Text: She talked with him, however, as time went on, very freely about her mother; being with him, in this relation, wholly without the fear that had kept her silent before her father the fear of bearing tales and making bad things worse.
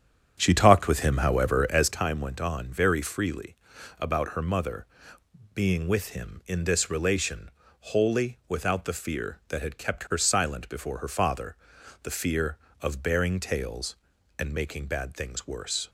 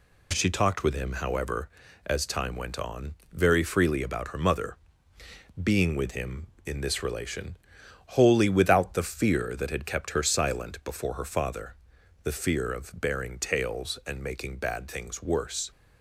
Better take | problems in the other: second | starts louder than the rest; strong; until 2.0 s; 8.5 dB // pauses between "freely" and "about"; at 3.5 s; 0.42 s long // pauses between "father" and "the"; noticeable; at 11.5 s; 0.46 s long; noticeable in the second

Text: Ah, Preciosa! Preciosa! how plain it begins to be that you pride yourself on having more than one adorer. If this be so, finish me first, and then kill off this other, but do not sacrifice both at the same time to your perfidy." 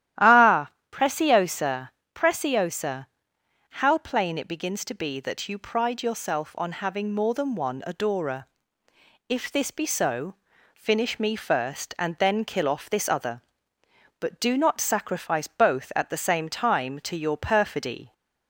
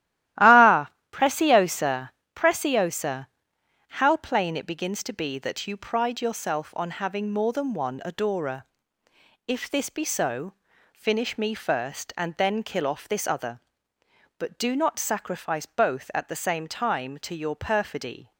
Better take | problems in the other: first | gets quieter; strong; throughout; 10 dB // starts louder than the rest; strong; until 1.6 s; 14 dB; strong in the first

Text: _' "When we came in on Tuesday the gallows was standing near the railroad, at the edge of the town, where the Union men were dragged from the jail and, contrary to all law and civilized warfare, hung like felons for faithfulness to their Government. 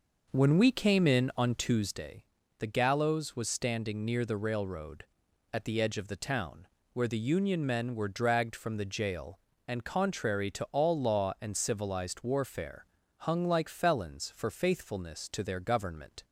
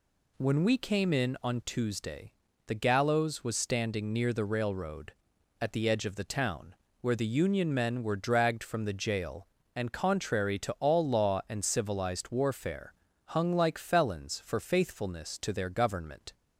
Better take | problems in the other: second | starts louder than the rest; noticeable; until 2.0 s; 5.5 dB // pauses between "Tuesday" and "the"; slight; at 2.2 s; 0.36 s long; slight in the second

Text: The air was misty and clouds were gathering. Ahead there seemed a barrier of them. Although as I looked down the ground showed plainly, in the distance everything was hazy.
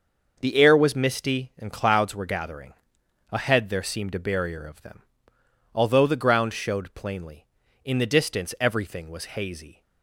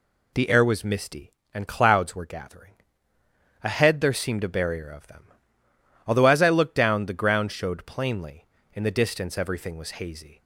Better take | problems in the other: second | skips "as I looked down"; at 6.0 s

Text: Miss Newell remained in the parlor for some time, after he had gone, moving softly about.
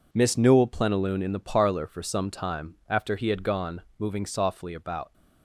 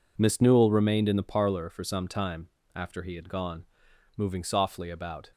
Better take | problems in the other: second | says "plenilune" for "remained"; at 0.6 s

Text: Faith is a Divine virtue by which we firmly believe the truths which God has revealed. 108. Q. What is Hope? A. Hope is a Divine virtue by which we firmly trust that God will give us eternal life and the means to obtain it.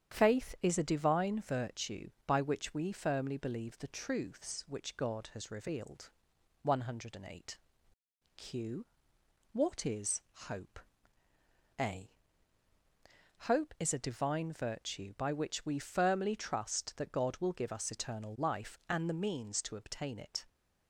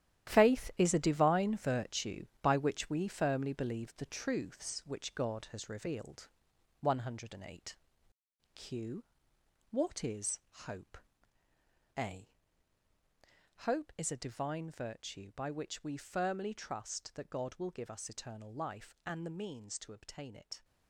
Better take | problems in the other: first | gets quieter; strong; throughout; 11 dB // starts louder than the rest; strong; until 1.3 s; 11.5 dB; strong in the first // pauses between "is" and "Hope"; slight; at 10.3 s; 0.28 s long; slight in the first

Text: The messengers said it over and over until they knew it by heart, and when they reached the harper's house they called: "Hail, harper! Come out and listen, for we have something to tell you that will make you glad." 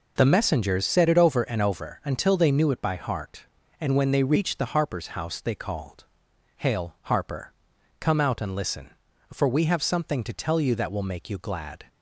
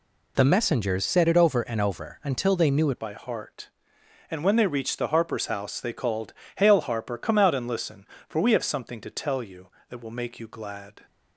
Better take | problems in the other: first | changes voice at "by"; from 3.0 s on; 8.0 s long

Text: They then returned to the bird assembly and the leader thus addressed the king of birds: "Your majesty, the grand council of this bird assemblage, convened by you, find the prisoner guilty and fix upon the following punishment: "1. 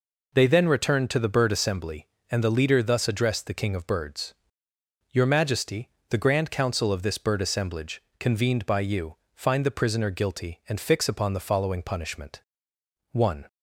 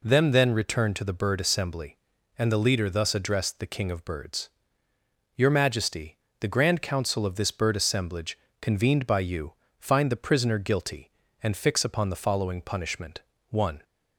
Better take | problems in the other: first | says "Them" for "They"; at 0.0 s

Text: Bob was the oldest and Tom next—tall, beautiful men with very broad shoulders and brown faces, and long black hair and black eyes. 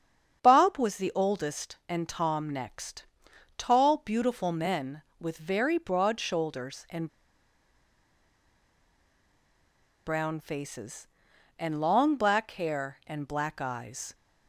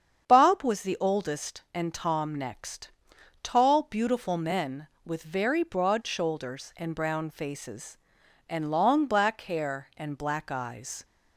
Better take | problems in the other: second | starts louder than the rest; strong; until 1.4 s; 7.5 dB; strong in the second // pauses between "and" and "brown"; strong; at 7.0 s; 2.9 s long

